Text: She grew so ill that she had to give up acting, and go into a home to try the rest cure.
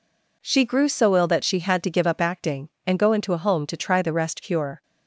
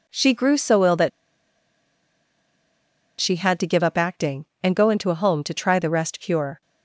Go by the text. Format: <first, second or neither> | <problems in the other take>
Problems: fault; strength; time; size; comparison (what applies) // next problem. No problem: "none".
first | pauses between "that" and "she"; strong; at 1.1 s; 2.1 s long